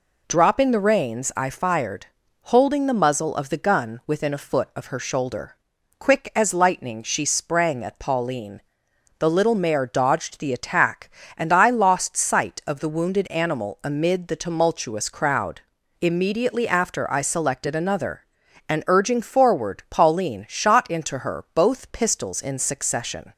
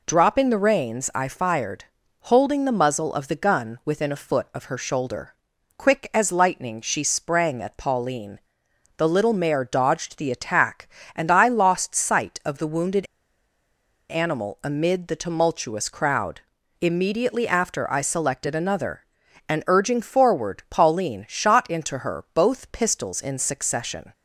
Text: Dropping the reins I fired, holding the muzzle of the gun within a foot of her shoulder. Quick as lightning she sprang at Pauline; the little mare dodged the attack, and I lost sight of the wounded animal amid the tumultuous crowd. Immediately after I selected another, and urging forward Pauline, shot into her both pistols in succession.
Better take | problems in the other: first | pauses between "wounded" and "animal"; at 13.0 s; 1.0 s long

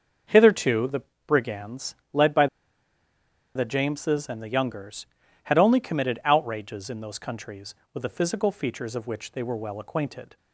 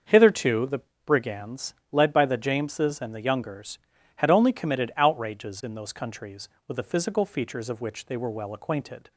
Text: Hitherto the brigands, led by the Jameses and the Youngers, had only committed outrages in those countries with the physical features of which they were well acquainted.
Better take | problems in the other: second | starts louder than the rest; until 1.5 s; 6.5 dB; also in the second // pauses between "the" and "brigands"; slight; at 1.0 s; 0.26 s long; slight in the second // pauses between "by" and "the"; at 2.4 s; 1.0 s long

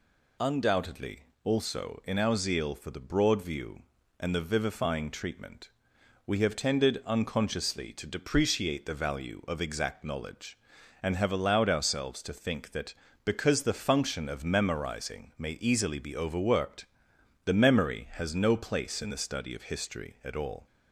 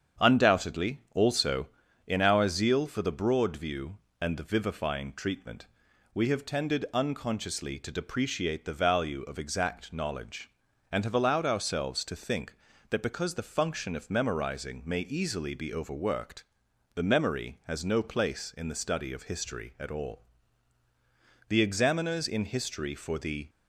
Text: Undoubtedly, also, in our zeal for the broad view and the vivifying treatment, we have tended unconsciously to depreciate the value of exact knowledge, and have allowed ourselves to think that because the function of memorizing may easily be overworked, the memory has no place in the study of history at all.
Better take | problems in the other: first | starts louder than the rest; strong; until 1.3 s; 8 dB // goes on to say "The examiners in history for the"; strong; from 21.4 s on; 2.0 s long

